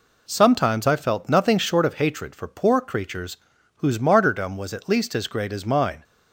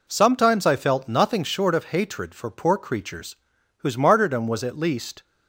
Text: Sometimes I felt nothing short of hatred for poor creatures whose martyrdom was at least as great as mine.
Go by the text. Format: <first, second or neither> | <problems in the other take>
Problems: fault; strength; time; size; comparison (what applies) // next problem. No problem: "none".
first | pauses between "creatures" and "whose"; at 3.3 s; 0.44 s long; also in the first // stops before "as great as mine"; at 5.2 s